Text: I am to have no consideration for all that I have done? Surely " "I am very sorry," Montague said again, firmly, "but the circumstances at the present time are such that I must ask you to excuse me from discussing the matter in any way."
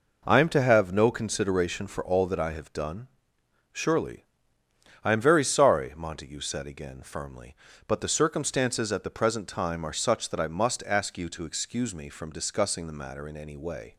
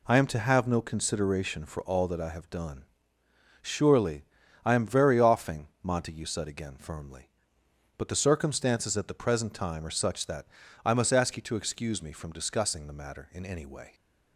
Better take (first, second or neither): first